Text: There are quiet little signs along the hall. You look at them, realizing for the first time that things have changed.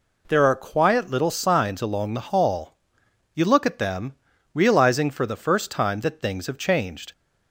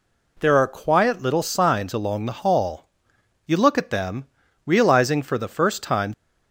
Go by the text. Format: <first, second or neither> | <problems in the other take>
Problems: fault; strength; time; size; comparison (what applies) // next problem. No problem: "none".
first | stops before "that things have changed"; at 6.1 s